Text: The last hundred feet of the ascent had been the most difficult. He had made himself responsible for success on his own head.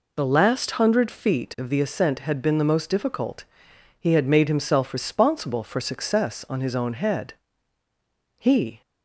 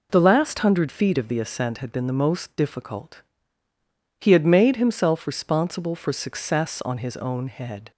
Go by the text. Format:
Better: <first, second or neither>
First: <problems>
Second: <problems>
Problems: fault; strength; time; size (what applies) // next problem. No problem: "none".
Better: second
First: goes on to say "He"; slight; from 8.3 s on; 0.42 s long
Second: none